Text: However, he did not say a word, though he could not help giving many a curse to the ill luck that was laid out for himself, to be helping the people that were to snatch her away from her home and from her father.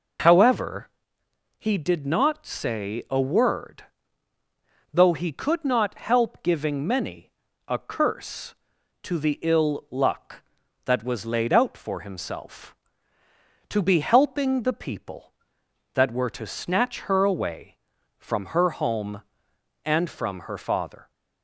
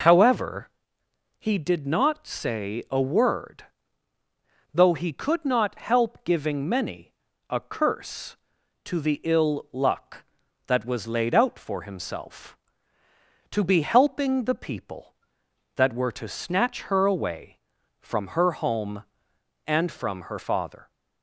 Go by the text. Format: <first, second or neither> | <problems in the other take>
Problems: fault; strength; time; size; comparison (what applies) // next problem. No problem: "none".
neither | pauses between "many" and "a"; the same in both